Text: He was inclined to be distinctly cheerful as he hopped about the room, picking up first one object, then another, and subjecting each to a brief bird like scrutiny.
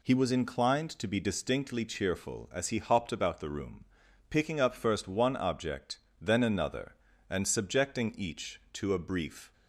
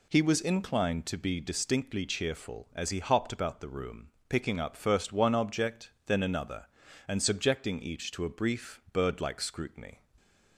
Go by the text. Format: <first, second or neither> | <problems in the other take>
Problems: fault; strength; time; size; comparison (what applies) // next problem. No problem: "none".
second | stops before "bird like scrutiny"; at 9.5 s